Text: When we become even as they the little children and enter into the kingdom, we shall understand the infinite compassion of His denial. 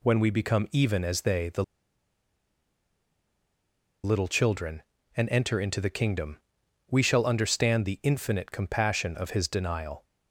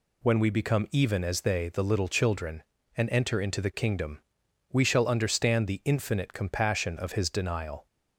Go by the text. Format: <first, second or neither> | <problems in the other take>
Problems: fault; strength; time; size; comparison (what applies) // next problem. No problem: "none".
second | pauses between "the" and "little"; strong; at 1.6 s; 2.4 s long